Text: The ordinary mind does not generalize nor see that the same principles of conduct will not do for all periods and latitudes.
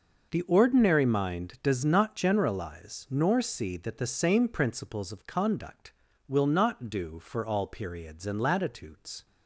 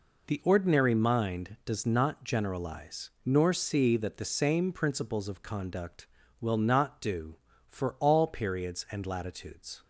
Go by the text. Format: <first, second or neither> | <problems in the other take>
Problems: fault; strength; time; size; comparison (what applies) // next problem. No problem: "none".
neither | none